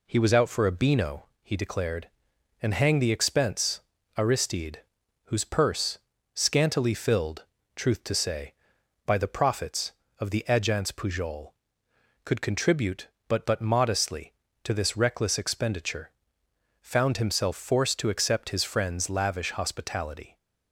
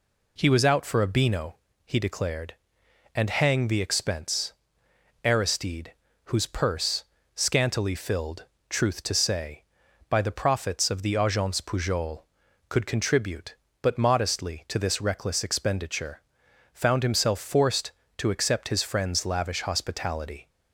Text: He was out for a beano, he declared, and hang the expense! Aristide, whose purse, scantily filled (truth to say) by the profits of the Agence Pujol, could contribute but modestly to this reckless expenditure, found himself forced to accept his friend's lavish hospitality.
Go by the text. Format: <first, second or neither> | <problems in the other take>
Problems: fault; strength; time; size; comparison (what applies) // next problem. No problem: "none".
second | says "but" twice; at 13.4 s